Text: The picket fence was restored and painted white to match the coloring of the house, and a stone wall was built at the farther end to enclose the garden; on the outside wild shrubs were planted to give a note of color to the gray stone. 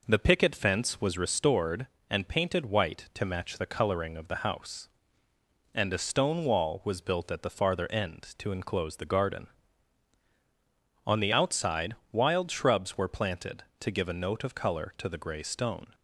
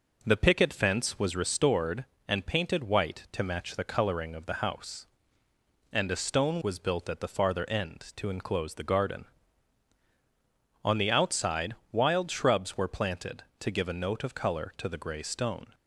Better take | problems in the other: first | skips "wall"; at 6.6 s // pauses between "outside" and "wild"; slight; at 11.7 s; 0.16 s long; slight in the first

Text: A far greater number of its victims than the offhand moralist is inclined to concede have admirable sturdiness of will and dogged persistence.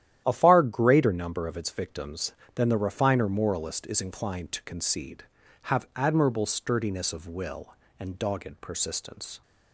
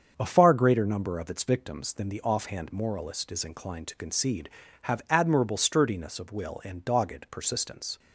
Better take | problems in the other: second | starts louder than the rest; strong; until 1.2 s; 11.5 dB; strong in the second // says "refiner" for "offhand"; at 2.7 s

